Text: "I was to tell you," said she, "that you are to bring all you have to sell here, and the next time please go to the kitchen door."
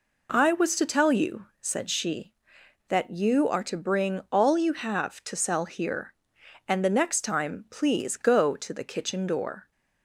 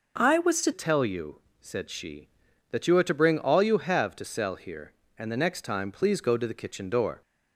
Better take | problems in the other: first | changes voice at "tell"; from 0.7 s on; 6.5 s long

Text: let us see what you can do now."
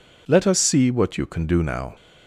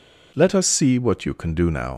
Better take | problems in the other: first | leaves "now" unfinished; at 1.9 s; 55 ms

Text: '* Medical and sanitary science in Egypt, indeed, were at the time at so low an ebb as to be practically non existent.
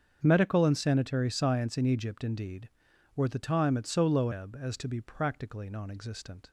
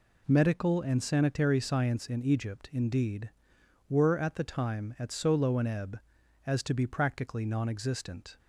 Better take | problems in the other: second | starts louder than the rest; strong; until 1.2 s; 7.5 dB // skips "an"; at 4.3 s

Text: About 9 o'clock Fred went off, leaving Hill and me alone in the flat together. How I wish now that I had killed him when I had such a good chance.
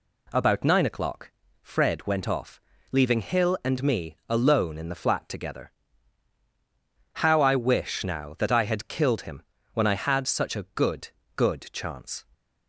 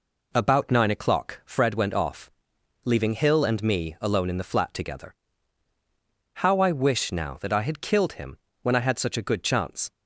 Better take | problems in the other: second | pauses between "o'clock" and "Fred"; slight; at 1.2 s; 0.32 s long // pauses between "him" and "when"; slight; at 9.4 s; 0.30 s long; slight in the second // says "good" twice; at 11.3 s

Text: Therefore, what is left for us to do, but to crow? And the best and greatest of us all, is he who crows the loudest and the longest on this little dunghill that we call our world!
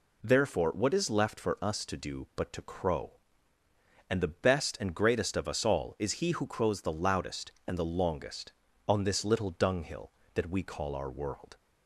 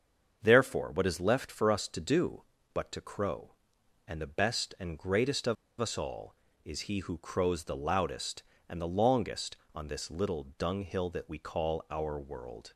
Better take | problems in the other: first | starts louder than the rest; until 1.4 s; 6.5 dB // pauses between "of" and "us"; slight; at 5.5 s; 0.25 s long

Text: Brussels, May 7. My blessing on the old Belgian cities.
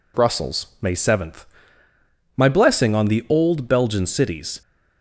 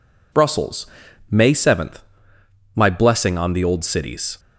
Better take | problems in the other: first | skips "Belgian"; at 3.8 s

